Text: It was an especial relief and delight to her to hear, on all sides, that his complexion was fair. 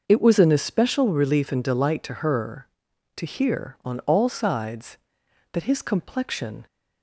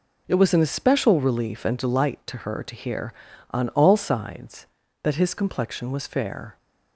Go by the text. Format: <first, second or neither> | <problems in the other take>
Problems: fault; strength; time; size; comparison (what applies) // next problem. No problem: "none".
second | starts louder than the rest; noticeable; until 1.0 s; 6 dB // stops before "was fair"; at 6.6 s